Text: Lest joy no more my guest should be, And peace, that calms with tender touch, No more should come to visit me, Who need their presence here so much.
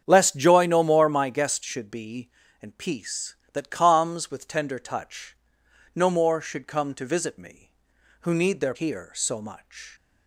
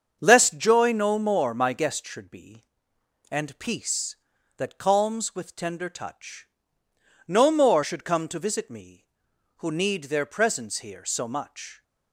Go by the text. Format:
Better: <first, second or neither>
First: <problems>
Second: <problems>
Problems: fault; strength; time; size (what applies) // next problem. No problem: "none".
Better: second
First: starts louder than the rest; strong; until 1.0 s; 8 dB // skips "presence"; at 8.7 s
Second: starts louder than the rest; until 1.2 s; 7 dB